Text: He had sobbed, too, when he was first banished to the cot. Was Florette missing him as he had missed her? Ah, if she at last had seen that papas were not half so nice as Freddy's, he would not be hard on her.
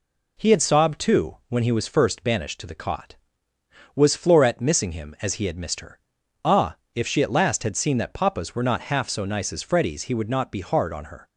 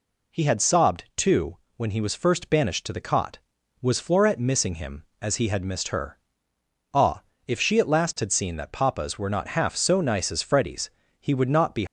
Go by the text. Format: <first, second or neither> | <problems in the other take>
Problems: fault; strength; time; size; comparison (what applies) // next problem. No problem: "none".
first | stops before "hard on her"; at 11.8 s